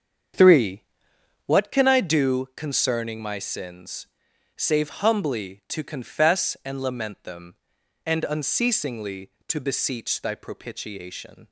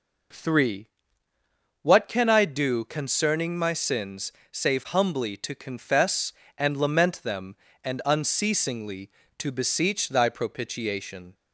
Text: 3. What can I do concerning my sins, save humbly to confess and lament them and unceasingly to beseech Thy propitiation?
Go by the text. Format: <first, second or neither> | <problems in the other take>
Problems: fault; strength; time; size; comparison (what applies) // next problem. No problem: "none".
second | starts louder than the rest; strong; until 1.7 s; 7.5 dB